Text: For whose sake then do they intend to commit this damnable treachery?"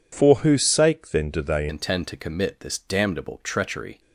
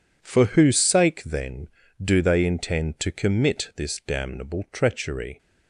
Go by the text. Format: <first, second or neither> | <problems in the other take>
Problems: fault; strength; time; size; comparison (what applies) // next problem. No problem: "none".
second | changes voice at "intend"; from 1.6 s on; 2.3 s long